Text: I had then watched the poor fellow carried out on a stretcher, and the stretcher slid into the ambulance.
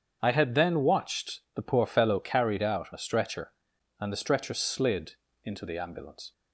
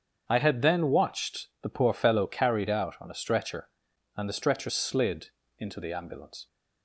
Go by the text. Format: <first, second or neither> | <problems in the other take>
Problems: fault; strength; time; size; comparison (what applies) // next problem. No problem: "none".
second | starts louder than the rest; strong; until 1.2 s; 7.5 dB; strong in the second // skips "on"; at 2.9 s // pauses between "slid" and "into"; slight; at 5.1 s; 0.30 s long; slight in the second